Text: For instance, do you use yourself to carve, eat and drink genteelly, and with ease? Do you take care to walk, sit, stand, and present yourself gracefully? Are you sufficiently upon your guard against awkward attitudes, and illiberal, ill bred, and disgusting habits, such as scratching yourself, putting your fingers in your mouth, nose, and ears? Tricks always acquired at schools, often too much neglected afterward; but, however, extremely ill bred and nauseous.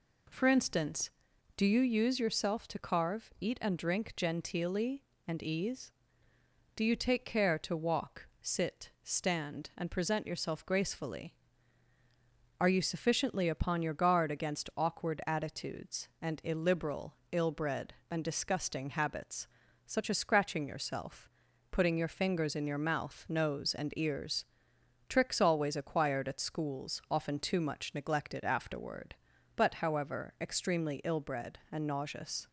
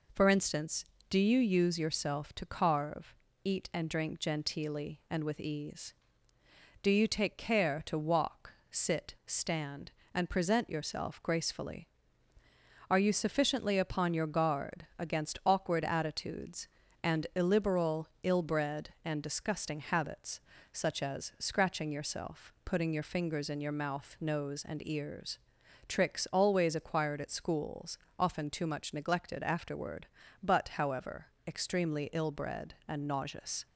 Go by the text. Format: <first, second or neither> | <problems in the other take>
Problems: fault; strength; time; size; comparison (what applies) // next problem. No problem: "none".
second | skips "with"; at 5.4 s